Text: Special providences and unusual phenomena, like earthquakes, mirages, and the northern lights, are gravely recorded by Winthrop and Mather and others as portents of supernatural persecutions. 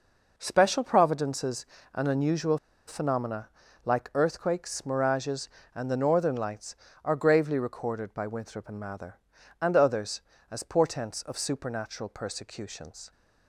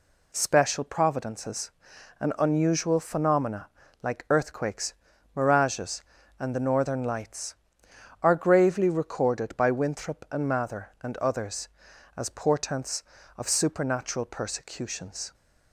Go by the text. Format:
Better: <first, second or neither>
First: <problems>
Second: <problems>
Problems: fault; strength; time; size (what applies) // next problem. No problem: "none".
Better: second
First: pauses between "unusual" and "phenomena"; slight; at 2.5 s; 0.29 s long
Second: none